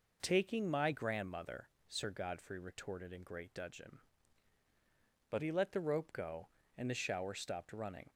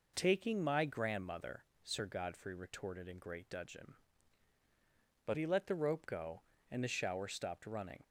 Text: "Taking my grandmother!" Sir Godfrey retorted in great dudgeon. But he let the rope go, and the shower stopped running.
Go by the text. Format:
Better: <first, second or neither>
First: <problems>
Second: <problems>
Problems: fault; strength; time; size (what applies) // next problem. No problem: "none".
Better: neither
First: none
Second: none